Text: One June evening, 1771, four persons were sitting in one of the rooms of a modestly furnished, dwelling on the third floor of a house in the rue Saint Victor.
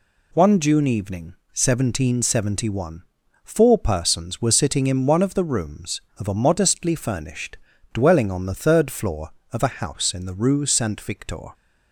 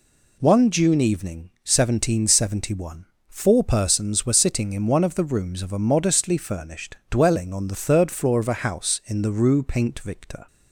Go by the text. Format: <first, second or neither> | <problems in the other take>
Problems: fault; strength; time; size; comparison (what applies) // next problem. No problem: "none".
first | says "Paint" for "Saint"; at 9.6 s